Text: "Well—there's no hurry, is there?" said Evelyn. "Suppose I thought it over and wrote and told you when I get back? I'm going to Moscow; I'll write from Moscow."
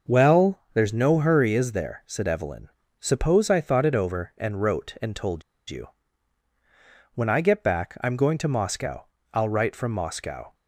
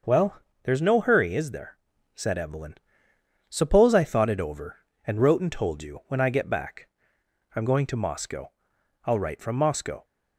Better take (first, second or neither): second